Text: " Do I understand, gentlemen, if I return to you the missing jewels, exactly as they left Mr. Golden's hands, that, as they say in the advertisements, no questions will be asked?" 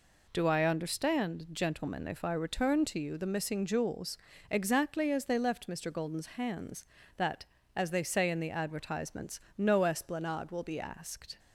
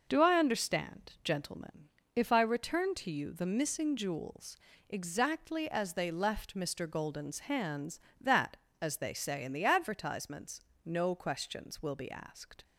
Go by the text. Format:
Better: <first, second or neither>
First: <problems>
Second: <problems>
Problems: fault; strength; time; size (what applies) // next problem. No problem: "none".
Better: second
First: says "esplanade" for "questions"; at 9.8 s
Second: none